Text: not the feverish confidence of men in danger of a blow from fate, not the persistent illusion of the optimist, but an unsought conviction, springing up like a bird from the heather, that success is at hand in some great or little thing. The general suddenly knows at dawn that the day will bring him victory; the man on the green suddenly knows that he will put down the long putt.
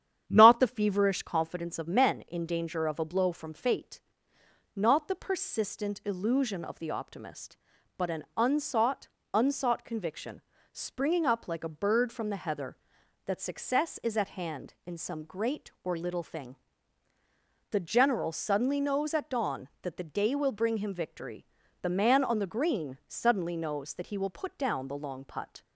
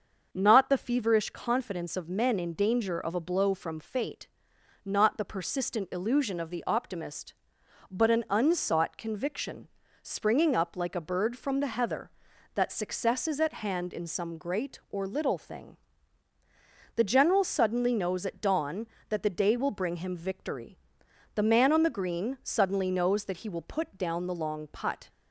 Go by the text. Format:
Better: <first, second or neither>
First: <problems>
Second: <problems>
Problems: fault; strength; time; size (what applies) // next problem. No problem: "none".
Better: second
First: starts louder than the rest; strong; until 1.2 s; 9.5 dB // says "unsought" twice; at 9.3 s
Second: starts louder than the rest; until 1.3 s; 6.5 dB